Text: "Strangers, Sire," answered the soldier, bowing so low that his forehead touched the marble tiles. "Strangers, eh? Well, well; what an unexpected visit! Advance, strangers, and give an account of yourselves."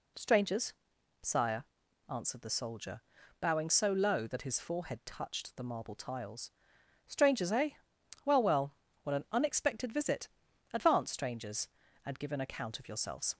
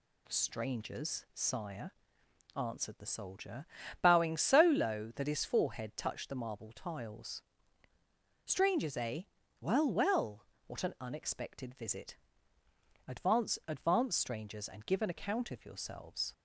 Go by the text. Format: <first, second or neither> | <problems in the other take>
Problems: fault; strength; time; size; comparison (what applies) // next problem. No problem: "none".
first | says "Advance" twice; at 13.6 s